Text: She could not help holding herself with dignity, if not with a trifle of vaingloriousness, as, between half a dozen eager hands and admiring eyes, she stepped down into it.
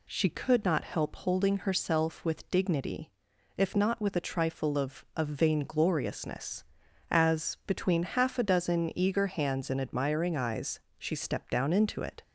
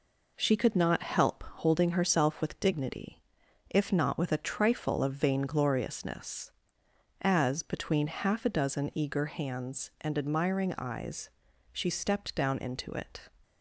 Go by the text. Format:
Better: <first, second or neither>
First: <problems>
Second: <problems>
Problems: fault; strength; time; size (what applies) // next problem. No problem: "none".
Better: second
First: says "of" twice; at 5.1 s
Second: none